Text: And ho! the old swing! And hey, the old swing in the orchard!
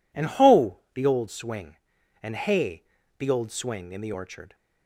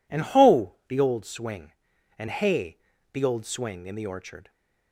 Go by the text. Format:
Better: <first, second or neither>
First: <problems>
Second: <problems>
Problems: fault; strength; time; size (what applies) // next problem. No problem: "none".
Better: neither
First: none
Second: none